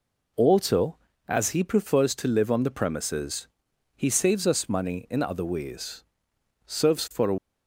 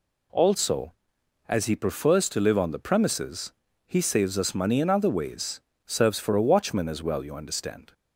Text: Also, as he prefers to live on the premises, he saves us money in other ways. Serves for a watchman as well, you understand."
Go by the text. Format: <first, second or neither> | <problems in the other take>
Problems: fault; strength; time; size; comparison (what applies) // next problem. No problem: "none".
second | stops before "watchman as well you understand"; at 7.3 s